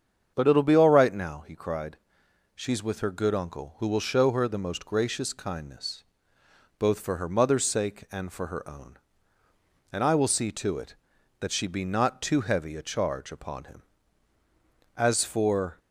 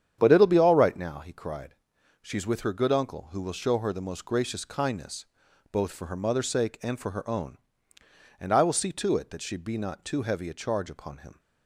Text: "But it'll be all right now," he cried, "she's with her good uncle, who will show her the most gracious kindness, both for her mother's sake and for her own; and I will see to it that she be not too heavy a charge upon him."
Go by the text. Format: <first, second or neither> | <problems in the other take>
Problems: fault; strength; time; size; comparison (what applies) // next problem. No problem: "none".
second | starts louder than the rest; strong; until 1.3 s; 7.5 dB; strong in the second // goes on to say "As for"; noticeable; from 14.9 s on; 0.82 s long